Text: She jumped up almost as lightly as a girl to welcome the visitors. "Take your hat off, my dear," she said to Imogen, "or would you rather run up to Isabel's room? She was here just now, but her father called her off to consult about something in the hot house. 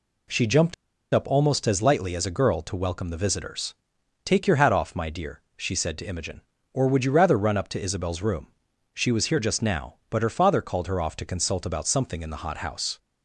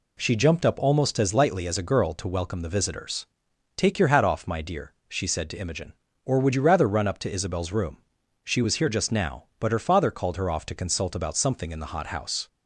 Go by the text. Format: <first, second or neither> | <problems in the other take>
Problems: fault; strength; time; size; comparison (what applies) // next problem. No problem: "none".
second | pauses between "jumped" and "up"; at 0.7 s; 0.39 s long